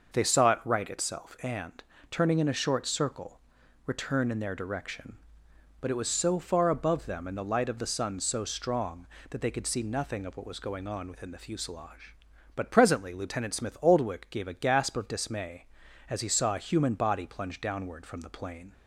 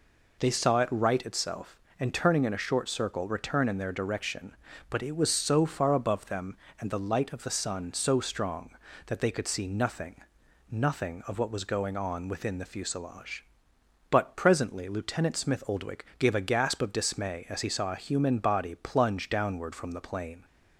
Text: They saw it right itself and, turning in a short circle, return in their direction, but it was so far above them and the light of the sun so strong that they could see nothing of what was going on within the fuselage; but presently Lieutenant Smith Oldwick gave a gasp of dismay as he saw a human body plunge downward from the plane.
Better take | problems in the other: first | says "nothing" twice; at 10.7 s

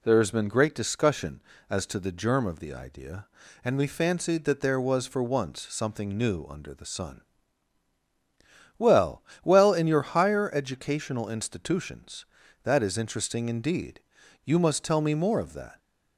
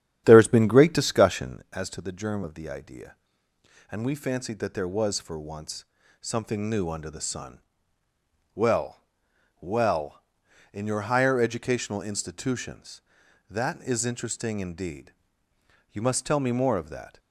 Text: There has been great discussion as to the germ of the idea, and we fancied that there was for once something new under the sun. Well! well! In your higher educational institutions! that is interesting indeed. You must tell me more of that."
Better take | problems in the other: first | starts louder than the rest; strong; until 1.6 s; 10 dB // pauses between "once" and "something"; slight; at 5.8 s; 0.36 s long

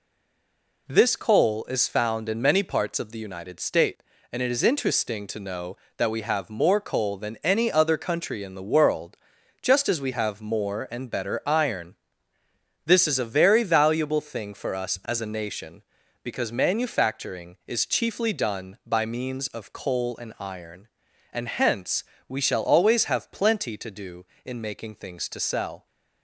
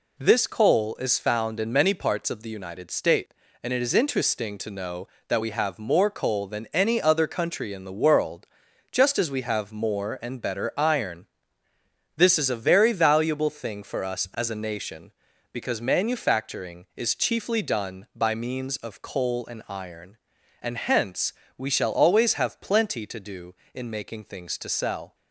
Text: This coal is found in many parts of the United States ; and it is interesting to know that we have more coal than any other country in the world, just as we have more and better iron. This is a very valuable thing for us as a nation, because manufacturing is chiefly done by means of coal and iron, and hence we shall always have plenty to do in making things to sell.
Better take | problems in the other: second | stays silent before the first word; slight; until 0.8 s; 0.8 s long // pauses between "hence" and "we"; slight; at 22.0 s; 0.24 s long; slight in the second

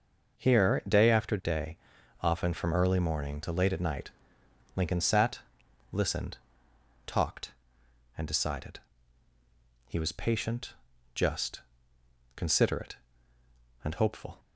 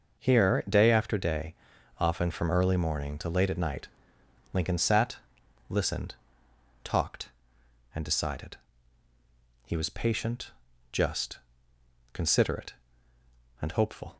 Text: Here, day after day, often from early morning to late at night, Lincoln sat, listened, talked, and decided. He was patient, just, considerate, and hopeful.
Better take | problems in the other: neither | none

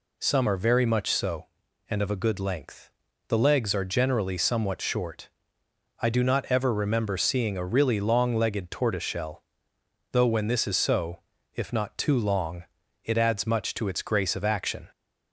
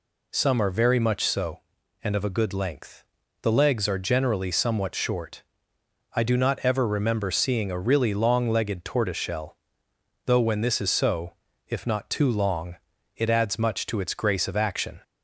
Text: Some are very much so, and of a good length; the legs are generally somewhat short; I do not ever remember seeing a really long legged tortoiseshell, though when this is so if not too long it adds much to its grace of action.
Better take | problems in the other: neither | pauses between "so" and "if"; the same in both // pauses between "long" and "it"; the same in both

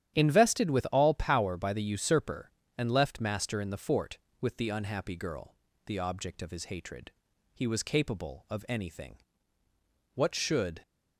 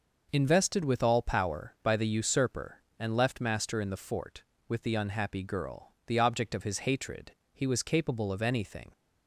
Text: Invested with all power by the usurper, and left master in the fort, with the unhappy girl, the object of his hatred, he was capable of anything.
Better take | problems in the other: second | starts louder than the rest; strong; until 1.2 s; 10.5 dB // goes on to say "What should"; noticeable; from 10.1 s on; 0.68 s long

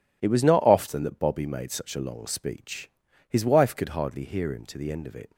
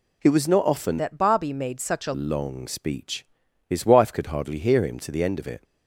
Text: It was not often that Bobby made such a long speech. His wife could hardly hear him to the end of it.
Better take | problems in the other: first | changes voice from "that" to "a"; from 0.9 to 2.1 s; 1.2 s long

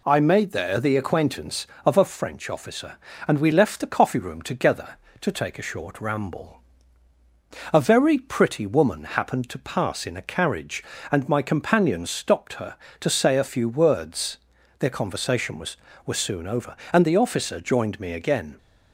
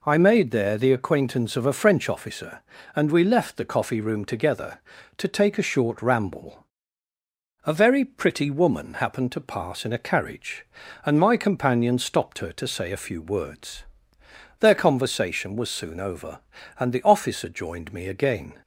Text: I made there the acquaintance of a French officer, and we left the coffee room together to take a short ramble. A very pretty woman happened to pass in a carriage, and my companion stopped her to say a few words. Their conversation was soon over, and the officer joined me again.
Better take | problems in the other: second | says "was" twice; at 16.0 s

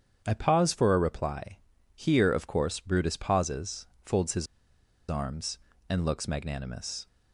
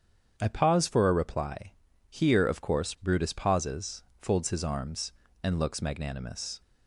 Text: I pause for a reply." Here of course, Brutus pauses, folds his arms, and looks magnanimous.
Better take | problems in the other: second | starts louder than the rest; strong; until 1.2 s; 8 dB; strong in the second // pauses between "his" and "arms"; noticeable; at 4.4 s; 0.64 s long

